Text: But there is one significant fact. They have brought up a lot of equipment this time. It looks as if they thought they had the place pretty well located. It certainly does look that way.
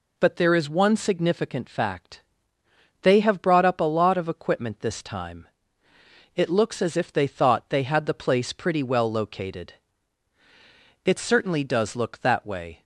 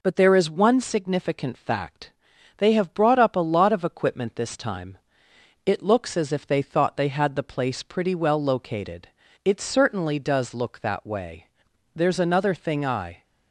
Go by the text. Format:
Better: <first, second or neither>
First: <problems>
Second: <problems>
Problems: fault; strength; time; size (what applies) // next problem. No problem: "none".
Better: first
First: none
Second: goes on to say "There's another thing I"; noticeable; from 11.9 s on; 1.2 s long